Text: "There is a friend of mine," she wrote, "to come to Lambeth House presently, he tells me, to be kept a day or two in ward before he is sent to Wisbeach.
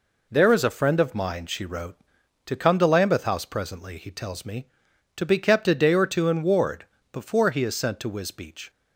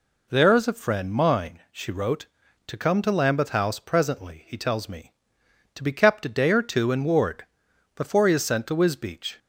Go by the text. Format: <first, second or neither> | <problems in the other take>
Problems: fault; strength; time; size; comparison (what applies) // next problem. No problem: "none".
first | skips "of"; at 1.1 s // pauses between "ward" and "before"; noticeable; at 7.4 s; 0.48 s long; slight in the first